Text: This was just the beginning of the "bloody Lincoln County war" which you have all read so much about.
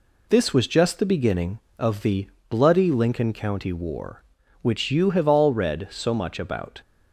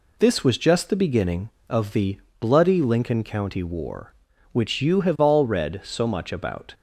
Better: neither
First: pauses between "the" and "bloody"; slight; at 2.2 s; 0.20 s long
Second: pauses between "the" and "bloody"; slight; at 2.1 s; 0.20 s long

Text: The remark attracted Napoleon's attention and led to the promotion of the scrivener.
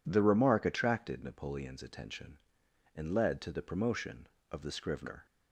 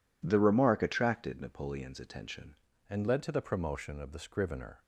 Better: first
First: none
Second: changes voice at "and"; from 2.8 s on; 2.0 s long

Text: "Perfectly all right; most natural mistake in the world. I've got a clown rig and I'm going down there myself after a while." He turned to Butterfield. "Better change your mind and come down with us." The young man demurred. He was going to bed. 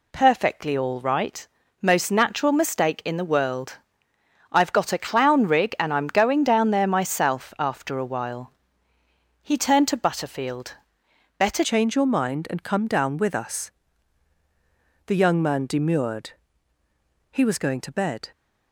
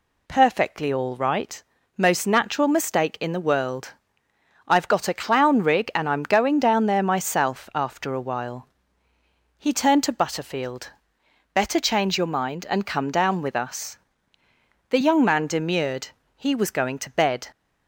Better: second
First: changes voice at "change"; from 11.6 s on; 6.7 s long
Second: none

